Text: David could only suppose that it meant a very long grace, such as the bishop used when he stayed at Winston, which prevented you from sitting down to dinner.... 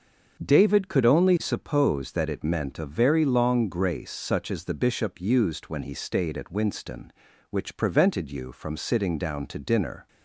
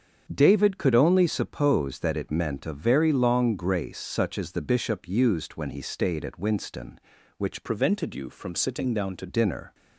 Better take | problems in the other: first | starts louder than the rest; strong; until 1.3 s; 7.5 dB; also in the first // changes voice from "prevented" to "to"; from 7.6 to 9.2 s; 1.6 s long

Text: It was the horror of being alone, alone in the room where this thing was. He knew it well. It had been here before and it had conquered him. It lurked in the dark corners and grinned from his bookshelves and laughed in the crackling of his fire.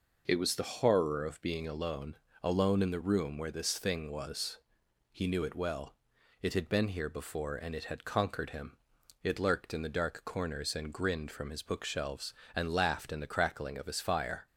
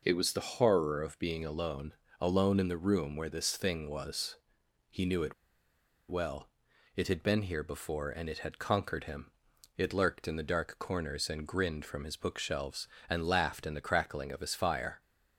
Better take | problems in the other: first | pauses between "it" and "well"; noticeable; at 5.3 s; 0.74 s long

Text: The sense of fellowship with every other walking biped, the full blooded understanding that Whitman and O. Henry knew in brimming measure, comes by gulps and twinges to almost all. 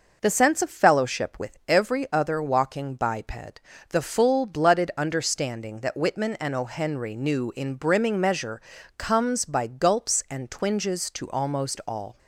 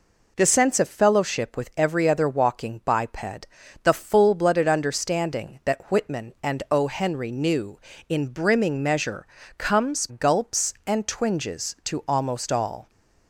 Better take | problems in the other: first | skips "by"; at 10.0 s

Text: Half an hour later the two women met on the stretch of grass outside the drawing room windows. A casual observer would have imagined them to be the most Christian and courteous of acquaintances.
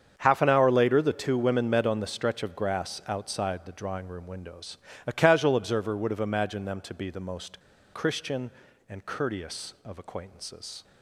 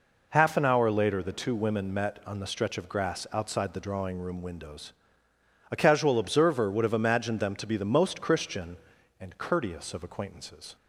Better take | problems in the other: second | starts louder than the rest; strong; until 1.1 s; 7.5 dB // pauses between "most" and "Christian"; slight; at 7.6 s; 0.32 s long

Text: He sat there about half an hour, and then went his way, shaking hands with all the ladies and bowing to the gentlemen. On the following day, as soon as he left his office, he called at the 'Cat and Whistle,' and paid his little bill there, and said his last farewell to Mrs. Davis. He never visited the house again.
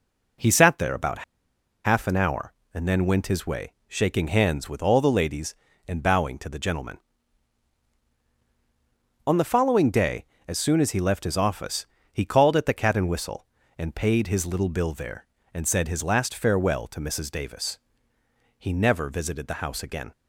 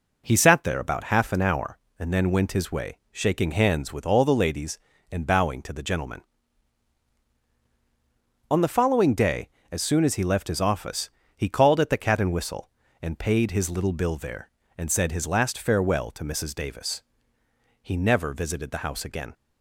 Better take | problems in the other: second | pauses between "about" and "half"; noticeable; at 1.2 s; 0.63 s long

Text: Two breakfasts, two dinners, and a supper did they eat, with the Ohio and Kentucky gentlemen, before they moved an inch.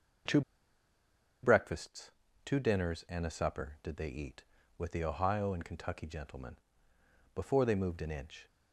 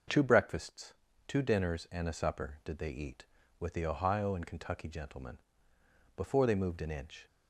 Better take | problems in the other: second | pauses between "Two" and "breakfasts"; at 0.4 s; 1.0 s long

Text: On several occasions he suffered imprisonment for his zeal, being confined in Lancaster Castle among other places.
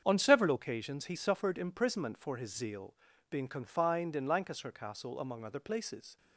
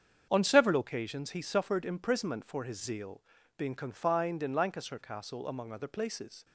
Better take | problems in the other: neither | starts louder than the rest; strong; the same in both

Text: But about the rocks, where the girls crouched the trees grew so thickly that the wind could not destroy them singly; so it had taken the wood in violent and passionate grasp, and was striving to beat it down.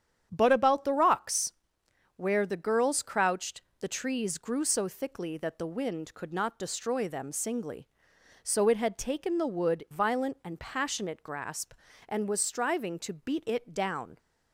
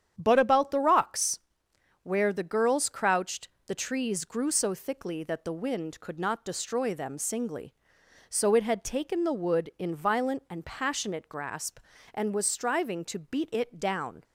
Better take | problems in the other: second | starts louder than the rest; strong; until 1.3 s; 9 dB; strong in the second // pauses between "crouched" and "the"; slight; at 3.6 s; 0.18 s long; slight in the second // skips "in"; at 9.8 s

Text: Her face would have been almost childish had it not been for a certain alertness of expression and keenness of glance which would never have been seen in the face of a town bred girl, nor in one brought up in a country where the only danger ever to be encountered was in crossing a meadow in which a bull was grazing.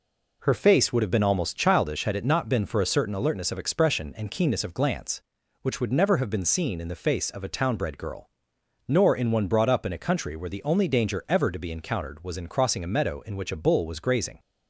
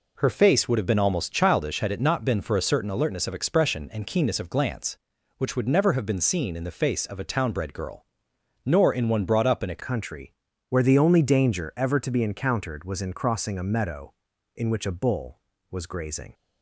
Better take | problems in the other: first | changes voice at "country"; from 9.8 s on; 6.5 s long // pauses between "country" and "where"; slight; at 10.3 s; 0.36 s long

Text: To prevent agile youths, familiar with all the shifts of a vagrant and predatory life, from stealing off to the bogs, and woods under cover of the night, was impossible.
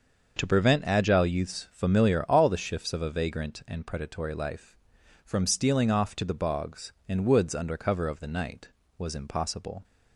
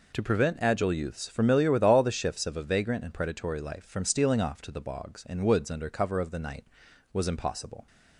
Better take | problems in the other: second | starts louder than the rest; until 1.4 s; 6.5 dB // skips "with"; at 2.2 s

